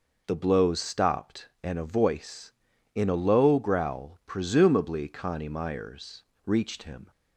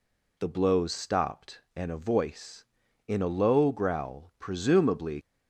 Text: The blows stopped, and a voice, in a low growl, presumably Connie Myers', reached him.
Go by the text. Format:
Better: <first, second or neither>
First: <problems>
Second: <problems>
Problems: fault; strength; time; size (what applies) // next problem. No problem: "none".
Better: first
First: none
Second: stops before "Connie Myers reached him"; at 5.2 s